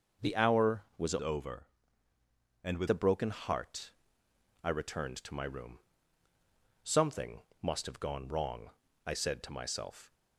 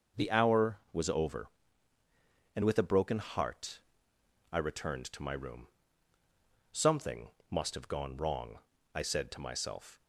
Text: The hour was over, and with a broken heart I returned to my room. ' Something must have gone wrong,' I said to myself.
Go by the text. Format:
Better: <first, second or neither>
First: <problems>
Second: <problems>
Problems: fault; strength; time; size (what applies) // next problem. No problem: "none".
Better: second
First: starts louder than the rest; until 1.4 s; 6.5 dB // changes voice from "over" to "with"; from 1.1 to 2.8 s; 1.7 s long // pauses between "heart" and "I"; noticeable; at 3.9 s; 0.72 s long // pauses between "Something" and "must"; slight; at 7.4 s; 0.18 s long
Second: starts louder than the rest; until 1.3 s; 6.5 dB // pauses between "heart" and "I"; noticeable; at 3.8 s; 0.72 s long // pauses between "Something" and "must"; slight; at 7.3 s; 0.18 s long